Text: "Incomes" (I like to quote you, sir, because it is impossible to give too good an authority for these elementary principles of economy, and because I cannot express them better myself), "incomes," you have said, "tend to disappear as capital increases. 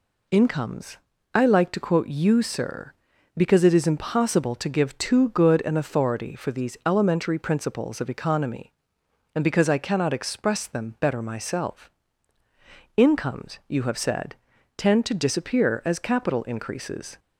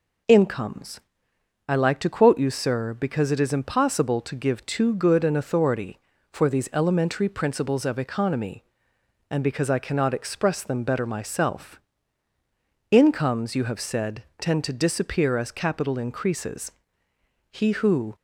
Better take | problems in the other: first | goes on to say "He who"; noticeable; from 17.5 s on; 0.64 s long

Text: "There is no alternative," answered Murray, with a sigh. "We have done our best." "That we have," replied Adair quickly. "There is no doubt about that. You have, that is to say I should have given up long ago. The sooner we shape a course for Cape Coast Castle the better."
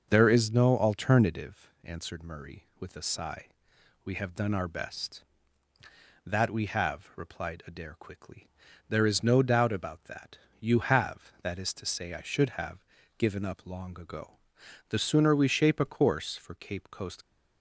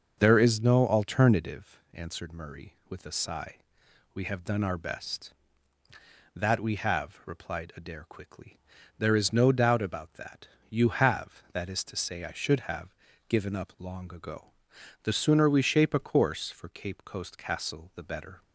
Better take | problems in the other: second | starts louder than the rest; until 1.1 s; 6 dB; also in the second // pauses between "have" and "given"; slight; at 12.8 s; 0.32 s long; slight in the second // stops before "Castle the better"; at 17.2 s

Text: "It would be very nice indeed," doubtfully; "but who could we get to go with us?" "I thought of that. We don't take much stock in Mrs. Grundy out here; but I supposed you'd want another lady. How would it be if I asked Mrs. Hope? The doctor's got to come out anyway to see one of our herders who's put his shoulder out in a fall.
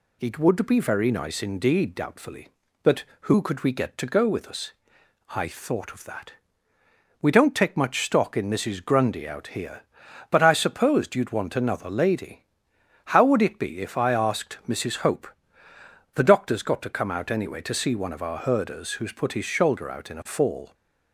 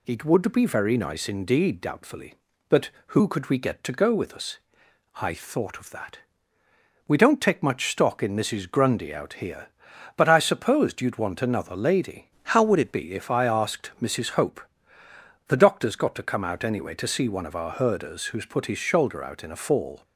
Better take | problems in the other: first | changes voice from "How" to "it"; from 12.4 to 12.9 s; 0.5 s long

